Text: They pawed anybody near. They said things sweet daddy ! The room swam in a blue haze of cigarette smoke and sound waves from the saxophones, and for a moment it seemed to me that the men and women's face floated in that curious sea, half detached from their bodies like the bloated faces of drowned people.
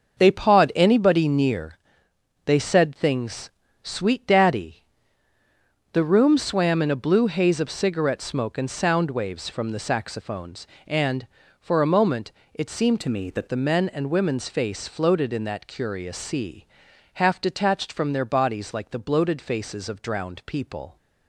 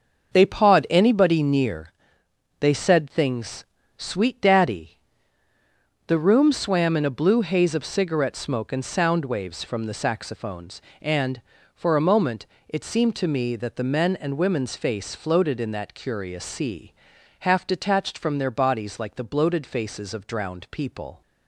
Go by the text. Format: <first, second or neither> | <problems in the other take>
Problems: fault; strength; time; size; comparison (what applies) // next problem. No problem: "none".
second | starts louder than the rest; until 1.2 s; 6.5 dB; also in the second // pauses between "things" and "sweet"; slight; at 3.4 s; 0.32 s long; slight in the second // pauses between "moment" and "it"; slight; at 12.3 s; 0.22 s long; slight in the second // changes voice from "to" to "that"; from 13.0 to 13.4 s; 0.4 s long